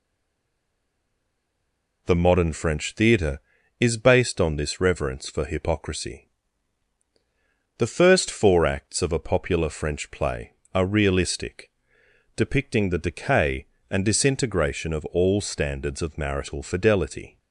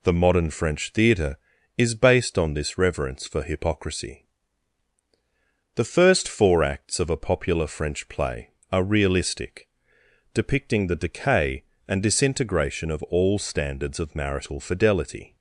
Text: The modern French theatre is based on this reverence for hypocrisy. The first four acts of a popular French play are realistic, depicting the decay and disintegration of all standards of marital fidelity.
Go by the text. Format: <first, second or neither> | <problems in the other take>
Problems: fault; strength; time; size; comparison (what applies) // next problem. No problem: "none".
second | stays silent before the first word; noticeable; until 2.0 s; 2.0 s long